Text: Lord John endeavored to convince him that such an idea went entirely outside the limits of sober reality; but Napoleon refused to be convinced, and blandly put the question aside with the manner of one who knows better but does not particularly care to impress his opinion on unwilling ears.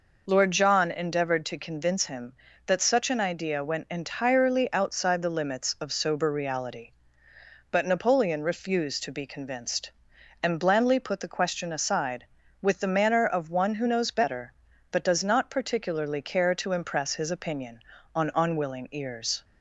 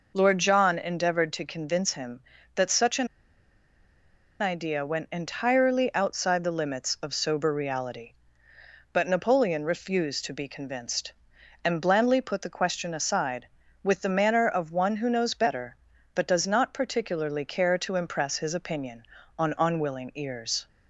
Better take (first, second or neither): first